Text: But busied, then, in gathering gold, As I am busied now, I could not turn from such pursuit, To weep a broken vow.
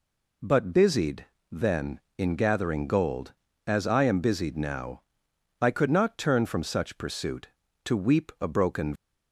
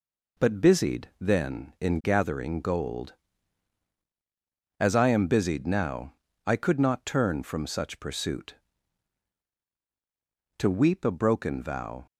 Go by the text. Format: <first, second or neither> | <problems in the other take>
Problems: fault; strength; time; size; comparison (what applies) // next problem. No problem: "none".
second | stops before "vow"; at 8.9 s